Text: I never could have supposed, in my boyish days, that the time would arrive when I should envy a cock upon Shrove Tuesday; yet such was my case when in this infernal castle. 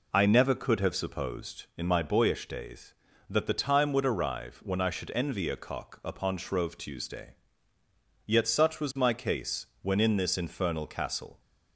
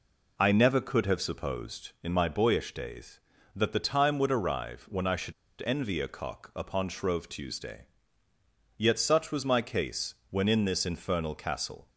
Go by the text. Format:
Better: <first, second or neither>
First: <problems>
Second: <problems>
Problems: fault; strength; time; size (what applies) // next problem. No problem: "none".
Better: first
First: pauses between "case" and "when"; slight; at 9.6 s; 0.16 s long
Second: pauses between "should" and "envy"; slight; at 5.3 s; 0.32 s long // pauses between "case" and "when"; slight; at 10.1 s; 0.16 s long